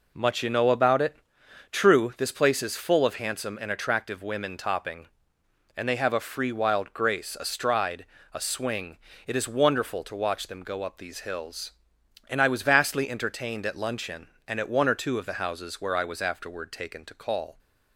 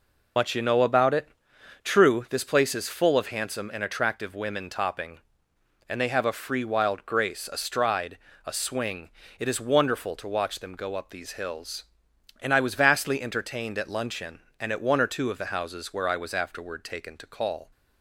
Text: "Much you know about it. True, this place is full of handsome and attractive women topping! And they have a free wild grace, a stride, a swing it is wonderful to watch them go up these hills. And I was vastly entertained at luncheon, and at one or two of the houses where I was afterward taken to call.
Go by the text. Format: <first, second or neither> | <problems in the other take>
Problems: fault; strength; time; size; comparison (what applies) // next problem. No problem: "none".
first | loses the start of "Much"; at 0.3 s; 85 ms // pauses between "swing" and "it"; slight; at 9.0 s; 0.30 s long; slight in the first